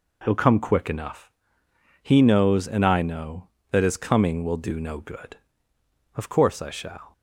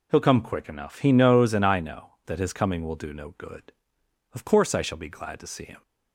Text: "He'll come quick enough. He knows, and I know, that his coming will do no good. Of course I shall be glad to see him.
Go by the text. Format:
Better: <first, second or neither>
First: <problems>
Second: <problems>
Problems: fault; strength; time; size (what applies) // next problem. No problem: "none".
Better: second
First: stops before "be glad to see him"; at 7.1 s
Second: none